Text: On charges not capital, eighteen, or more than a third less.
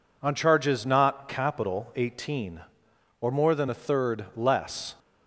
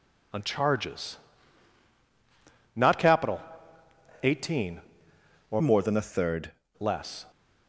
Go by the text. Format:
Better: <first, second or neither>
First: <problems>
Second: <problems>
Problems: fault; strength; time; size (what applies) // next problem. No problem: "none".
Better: first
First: none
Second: pauses between "charges" and "not"; strong; at 1.1 s; 1.5 s long // changes voice from "more" to "third"; from 5.6 to 6.5 s; 0.9 s long